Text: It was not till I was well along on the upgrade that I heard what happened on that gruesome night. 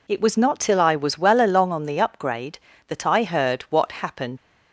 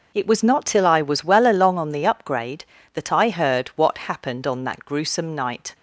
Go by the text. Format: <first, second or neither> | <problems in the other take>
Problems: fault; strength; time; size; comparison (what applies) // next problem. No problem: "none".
second | stops before "on that gruesome night"; at 4.3 s